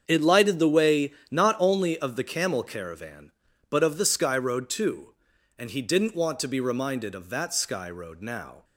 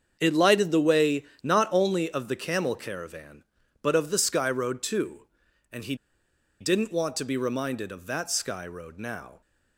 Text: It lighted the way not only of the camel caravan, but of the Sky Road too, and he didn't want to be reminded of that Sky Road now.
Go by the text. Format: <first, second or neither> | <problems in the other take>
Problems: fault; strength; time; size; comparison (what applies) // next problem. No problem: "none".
first | starts louder than the rest; strong; until 1.2 s; 7 dB; strong in the first // pauses between "way" and "not"; slight; at 1.2 s; 0.18 s long; slight in the first // pauses between "he" and "didn't"; noticeable; at 5.9 s; 0.64 s long